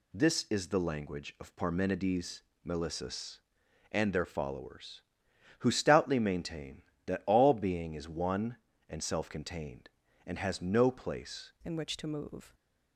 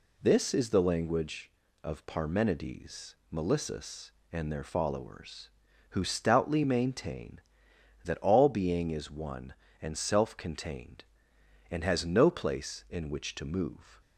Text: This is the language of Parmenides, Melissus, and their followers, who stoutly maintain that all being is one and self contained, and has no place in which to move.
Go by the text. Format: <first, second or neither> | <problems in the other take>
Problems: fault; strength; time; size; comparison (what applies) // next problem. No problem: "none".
second | changes voice at "in"; from 11.6 s on; 0.9 s long